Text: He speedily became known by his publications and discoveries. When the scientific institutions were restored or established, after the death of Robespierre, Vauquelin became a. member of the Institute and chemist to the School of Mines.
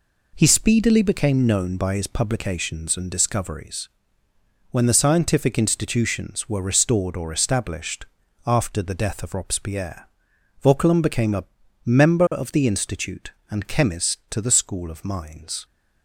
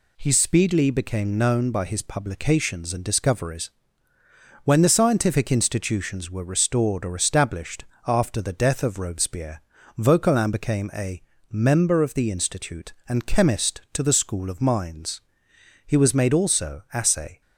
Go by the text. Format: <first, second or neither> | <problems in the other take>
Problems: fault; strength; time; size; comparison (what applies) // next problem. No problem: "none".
first | goes on to say "He was made also assay"; from 15.8 s on; 1.5 s long